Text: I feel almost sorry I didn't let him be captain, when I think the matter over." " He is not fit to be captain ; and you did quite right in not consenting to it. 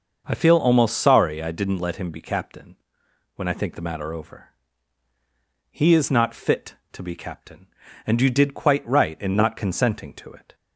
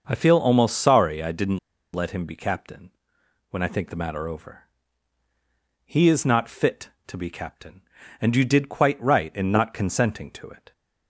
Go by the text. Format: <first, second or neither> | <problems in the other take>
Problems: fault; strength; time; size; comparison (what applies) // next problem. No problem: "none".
first | starts louder than the rest; until 1.0 s; 6 dB; also in the first // pauses between "didn't" and "let"; slight; at 1.5 s; 0.35 s long